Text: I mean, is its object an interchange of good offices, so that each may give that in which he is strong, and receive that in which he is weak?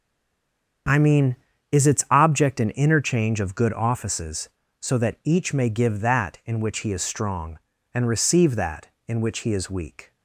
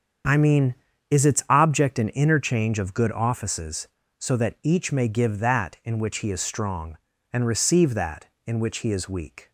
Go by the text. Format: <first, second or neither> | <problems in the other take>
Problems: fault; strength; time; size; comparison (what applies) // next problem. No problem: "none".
second | stays silent before the first word; slight; until 0.8 s; 0.8 s long // starts louder than the rest; strong; until 2.2 s; 7.5 dB; strong in the second